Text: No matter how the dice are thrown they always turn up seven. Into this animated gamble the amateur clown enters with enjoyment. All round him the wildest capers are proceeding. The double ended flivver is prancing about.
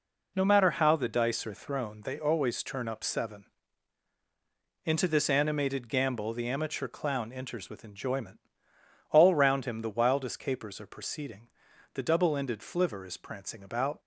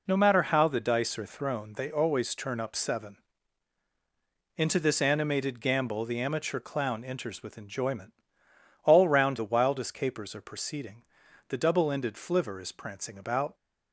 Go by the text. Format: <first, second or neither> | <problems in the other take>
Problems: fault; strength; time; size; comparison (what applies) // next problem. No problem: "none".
first | skips "him"; at 9.3 s